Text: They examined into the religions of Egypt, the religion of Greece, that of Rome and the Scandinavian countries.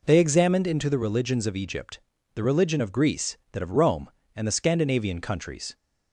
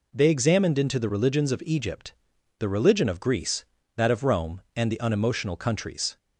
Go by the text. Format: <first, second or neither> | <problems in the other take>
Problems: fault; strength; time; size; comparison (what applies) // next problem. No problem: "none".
first | says "Unemotional" for "Scandinavian"; at 4.9 s